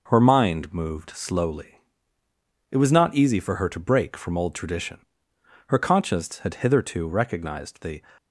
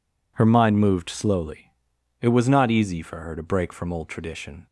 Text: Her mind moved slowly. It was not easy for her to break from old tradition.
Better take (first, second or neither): second